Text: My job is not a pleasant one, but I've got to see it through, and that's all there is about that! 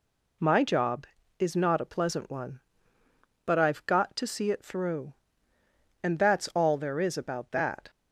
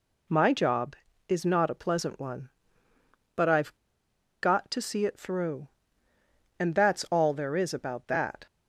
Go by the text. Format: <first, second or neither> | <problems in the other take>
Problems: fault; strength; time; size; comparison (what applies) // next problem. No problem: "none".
first | pauses between "I've" and "got"; noticeable; at 3.7 s; 0.66 s long